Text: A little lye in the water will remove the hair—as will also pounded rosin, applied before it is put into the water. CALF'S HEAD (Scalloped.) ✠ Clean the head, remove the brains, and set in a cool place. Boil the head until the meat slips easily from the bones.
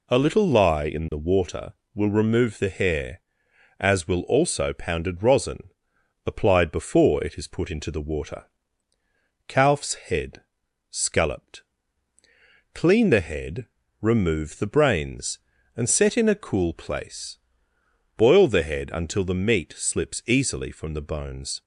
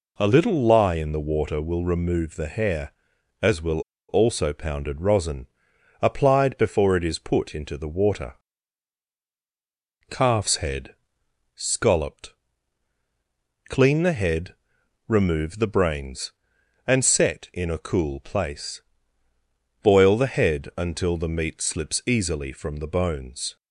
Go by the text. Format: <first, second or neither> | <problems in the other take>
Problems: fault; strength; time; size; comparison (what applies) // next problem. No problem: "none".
first | pauses between "will" and "also"; slight; at 3.7 s; 0.29 s long